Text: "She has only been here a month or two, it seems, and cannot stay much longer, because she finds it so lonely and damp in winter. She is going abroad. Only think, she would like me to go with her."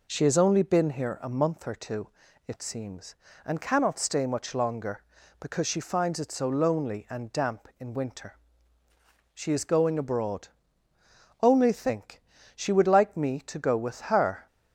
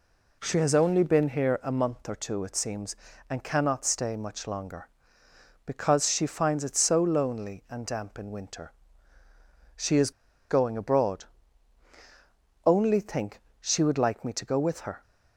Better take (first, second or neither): first